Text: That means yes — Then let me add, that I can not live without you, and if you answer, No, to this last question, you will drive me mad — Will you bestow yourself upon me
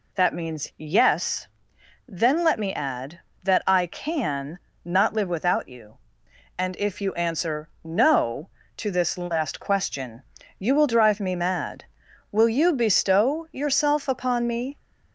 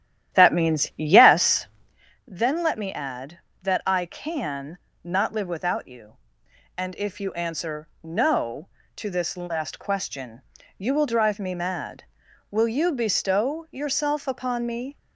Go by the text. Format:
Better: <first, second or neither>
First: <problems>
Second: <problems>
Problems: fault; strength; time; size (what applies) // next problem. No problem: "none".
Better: first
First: pauses between "can" and "not"; slight; at 4.5 s; 0.26 s long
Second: starts louder than the rest; strong; until 2.0 s; 11.5 dB // pauses between "can" and "not"; slight; at 4.7 s; 0.26 s long